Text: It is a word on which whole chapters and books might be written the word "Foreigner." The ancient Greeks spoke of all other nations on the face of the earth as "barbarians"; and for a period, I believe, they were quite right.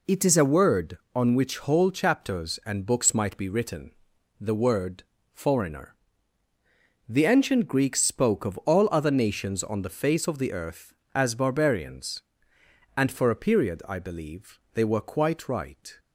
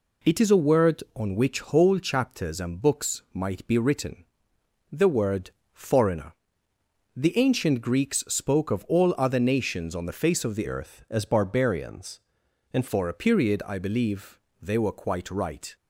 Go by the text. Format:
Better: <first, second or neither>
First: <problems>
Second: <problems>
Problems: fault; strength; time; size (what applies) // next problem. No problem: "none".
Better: first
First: pauses between "written" and "the"; noticeable; at 3.8 s; 0.50 s long // pauses between "word" and "Foreigner"; slight; at 5.0 s; 0.32 s long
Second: pauses between "written" and "the"; noticeable; at 4.2 s; 0.68 s long // pauses between "word" and "Foreigner"; slight; at 5.4 s; 0.24 s long // changes voice from "earth" to "and"; from 10.6 to 12.8 s; 2.2 s long